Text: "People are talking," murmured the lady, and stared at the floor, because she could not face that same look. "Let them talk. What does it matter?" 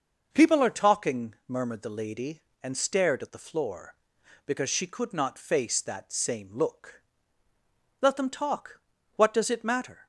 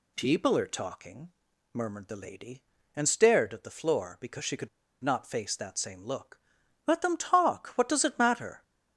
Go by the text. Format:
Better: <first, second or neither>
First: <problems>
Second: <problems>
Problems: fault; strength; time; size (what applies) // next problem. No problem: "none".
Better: first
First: none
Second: pauses between "could" and "not"; slight; at 4.6 s; 0.33 s long